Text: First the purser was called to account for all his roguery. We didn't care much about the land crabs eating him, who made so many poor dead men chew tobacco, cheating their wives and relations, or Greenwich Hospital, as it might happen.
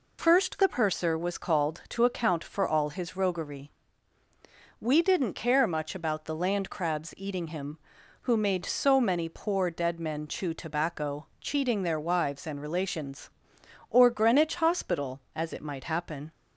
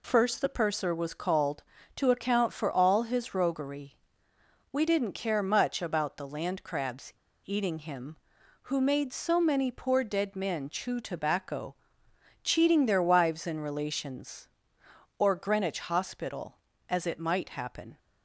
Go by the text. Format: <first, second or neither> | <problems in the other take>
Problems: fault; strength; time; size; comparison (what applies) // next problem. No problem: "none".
first | pauses between "crabs" and "eating"; slight; at 7.1 s; 0.34 s long